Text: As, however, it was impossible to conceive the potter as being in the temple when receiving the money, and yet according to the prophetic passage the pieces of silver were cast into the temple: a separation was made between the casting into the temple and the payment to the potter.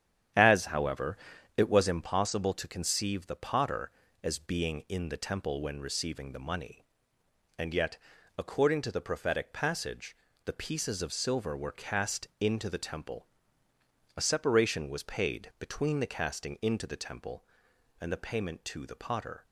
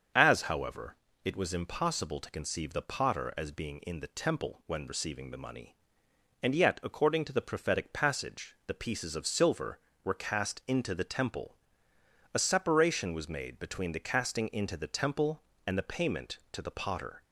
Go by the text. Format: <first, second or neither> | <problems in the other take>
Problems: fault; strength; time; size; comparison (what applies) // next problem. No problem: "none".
second | starts louder than the rest; strong; until 1.7 s; 9.5 dB; also in the second // pauses between "yet" and "according"; at 7.9 s; 0.38 s long // pauses between "passage" and "the"; slight; at 10.1 s; 0.30 s long // says "paid" for "made"; at 15.0 s